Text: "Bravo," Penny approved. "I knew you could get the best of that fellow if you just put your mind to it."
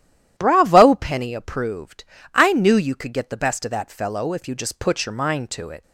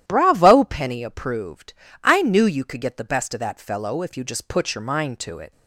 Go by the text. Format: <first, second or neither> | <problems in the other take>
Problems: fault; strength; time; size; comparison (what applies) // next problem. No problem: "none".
neither | starts louder than the rest; strong; the same in both